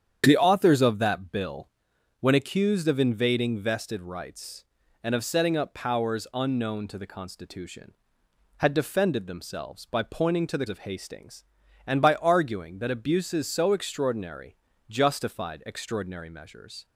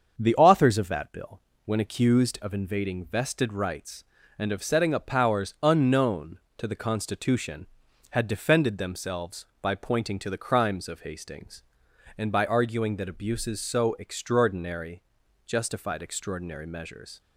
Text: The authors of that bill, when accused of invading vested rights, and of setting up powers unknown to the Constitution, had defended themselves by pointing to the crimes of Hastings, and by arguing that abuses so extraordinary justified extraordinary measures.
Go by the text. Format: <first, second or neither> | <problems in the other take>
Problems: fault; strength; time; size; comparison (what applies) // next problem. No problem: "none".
second | starts louder than the rest; strong; until 1.2 s; 8.5 dB; also in the second // skips "crimes"; at 10.6 s // pauses between "extraordinary" and "justified"; slight; at 14.5 s; 0.34 s long; also in the second